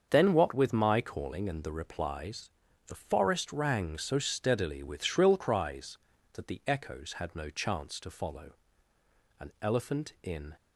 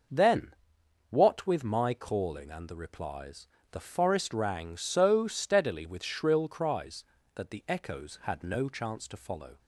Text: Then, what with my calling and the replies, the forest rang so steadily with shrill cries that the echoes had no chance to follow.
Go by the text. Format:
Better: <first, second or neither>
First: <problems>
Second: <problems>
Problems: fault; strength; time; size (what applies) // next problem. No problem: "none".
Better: second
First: starts louder than the rest; until 1.1 s; 6.5 dB // goes on to say "An elephant in"; noticeable; from 9.3 s on; 1.1 s long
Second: none